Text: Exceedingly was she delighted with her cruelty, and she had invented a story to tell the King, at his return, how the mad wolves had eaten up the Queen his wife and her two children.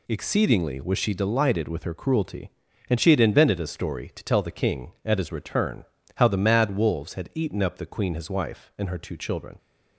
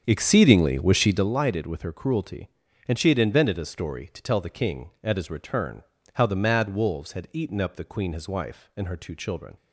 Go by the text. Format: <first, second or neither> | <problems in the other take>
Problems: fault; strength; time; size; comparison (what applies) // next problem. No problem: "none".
first | starts louder than the rest; strong; until 1.4 s; 7.5 dB